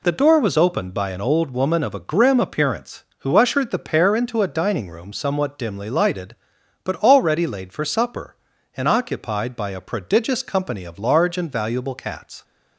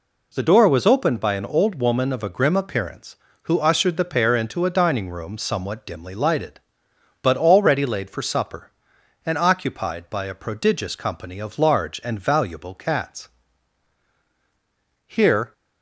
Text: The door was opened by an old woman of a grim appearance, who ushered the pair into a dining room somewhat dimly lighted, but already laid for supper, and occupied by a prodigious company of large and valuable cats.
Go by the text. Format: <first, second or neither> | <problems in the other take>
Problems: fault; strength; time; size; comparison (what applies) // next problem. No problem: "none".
first | goes on to say "Here"; slight; from 15.0 s on; 0.46 s long